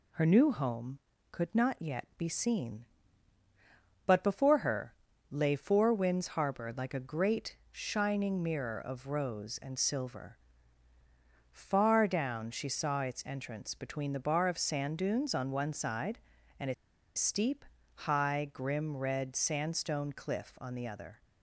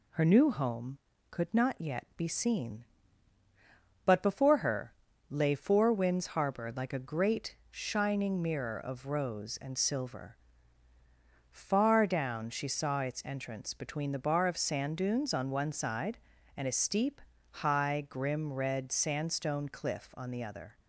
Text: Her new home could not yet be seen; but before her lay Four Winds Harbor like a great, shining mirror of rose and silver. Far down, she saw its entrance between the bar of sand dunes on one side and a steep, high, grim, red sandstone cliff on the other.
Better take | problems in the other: second | pauses between "her" and "lay"; slight; at 4.9 s; 0.36 s long; slight in the second // pauses between "a" and "steep"; at 16.7 s; 0.42 s long

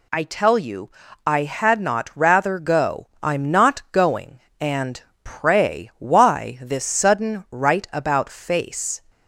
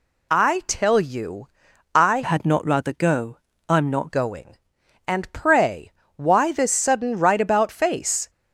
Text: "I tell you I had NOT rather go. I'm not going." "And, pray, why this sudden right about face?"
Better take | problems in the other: first | pauses between "you" and "I"; noticeable; at 1.4 s; 0.48 s long; also in the first // changes voice from "had" to "not"; from 2.2 to 4.1 s; 1.9 s long

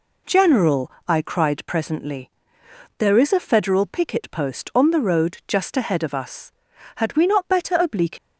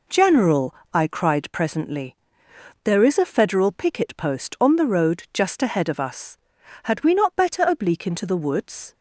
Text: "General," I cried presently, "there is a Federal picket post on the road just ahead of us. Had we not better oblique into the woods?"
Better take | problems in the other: second | stops before "into the woods"; at 8.1 s

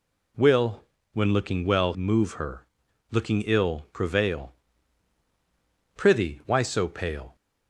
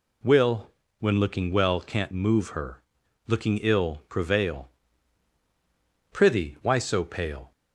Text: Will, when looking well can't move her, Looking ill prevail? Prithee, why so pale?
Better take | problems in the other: second | skips "can't"; at 1.9 s

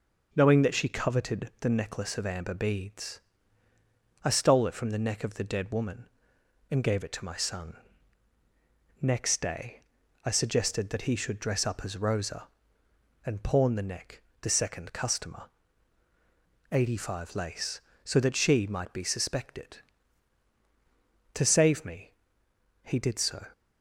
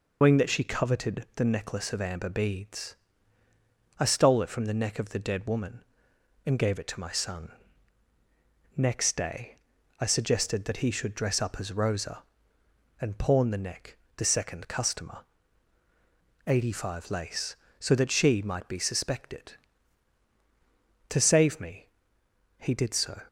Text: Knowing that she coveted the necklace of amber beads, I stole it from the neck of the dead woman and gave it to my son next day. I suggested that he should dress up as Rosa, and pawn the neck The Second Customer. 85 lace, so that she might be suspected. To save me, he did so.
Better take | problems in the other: first | loses the start of "Knowing"; at 0.2 s; 125 ms // pauses between "son" and "next"; strong; at 7.5 s; 1.2 s long; strong in the first // pauses between "neck" and "The"; slight; at 13.9 s; 0.20 s long; slight in the first

